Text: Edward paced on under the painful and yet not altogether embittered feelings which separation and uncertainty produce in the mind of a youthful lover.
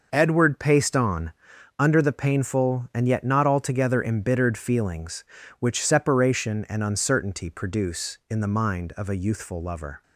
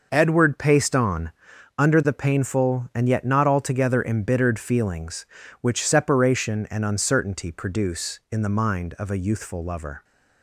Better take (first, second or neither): neither